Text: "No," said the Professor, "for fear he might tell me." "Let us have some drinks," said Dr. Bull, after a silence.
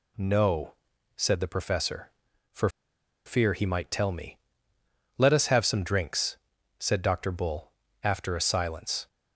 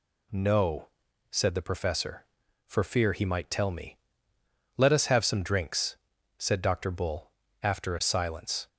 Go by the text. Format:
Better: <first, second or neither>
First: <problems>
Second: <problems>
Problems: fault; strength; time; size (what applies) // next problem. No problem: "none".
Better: second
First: pauses between "for" and "fear"; noticeable; at 2.6 s; 0.57 s long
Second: none